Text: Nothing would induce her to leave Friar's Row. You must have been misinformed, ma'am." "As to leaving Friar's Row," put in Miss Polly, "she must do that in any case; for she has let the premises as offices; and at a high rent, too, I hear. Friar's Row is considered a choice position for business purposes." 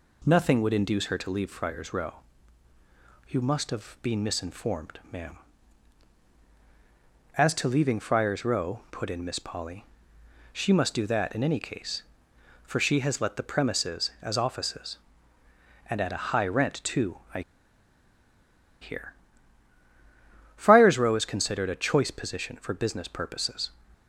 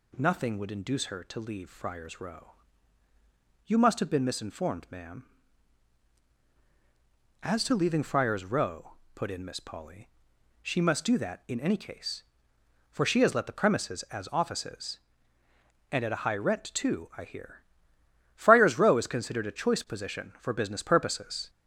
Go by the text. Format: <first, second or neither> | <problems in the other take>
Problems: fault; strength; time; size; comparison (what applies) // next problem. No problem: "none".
second | pauses between "I" and "hear"; strong; at 17.4 s; 1.4 s long